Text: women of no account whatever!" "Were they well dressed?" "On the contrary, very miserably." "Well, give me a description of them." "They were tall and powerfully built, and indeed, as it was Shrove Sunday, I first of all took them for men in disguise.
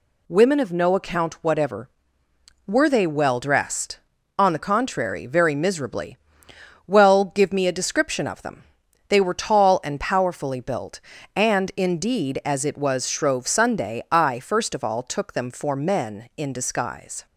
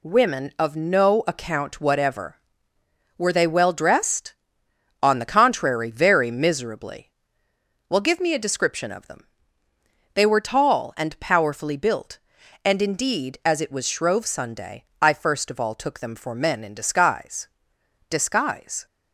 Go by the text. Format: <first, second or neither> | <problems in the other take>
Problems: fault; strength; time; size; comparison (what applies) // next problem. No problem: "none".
first | says "disguise" twice; at 18.0 s